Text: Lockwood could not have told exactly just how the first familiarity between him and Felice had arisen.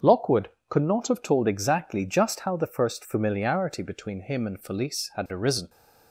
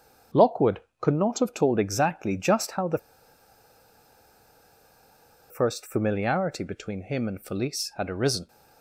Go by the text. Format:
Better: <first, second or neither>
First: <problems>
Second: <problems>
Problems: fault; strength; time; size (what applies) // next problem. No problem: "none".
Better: first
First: starts louder than the rest; until 1.2 s; 7 dB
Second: starts louder than the rest; strong; until 1.5 s; 7 dB // pauses between "the" and "first"; strong; at 2.9 s; 2.5 s long